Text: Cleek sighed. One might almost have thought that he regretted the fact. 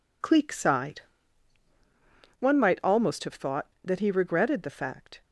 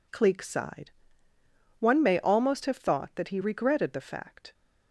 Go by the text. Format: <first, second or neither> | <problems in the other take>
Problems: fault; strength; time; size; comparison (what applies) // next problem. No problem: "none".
first | says "may" for "might"; at 2.0 s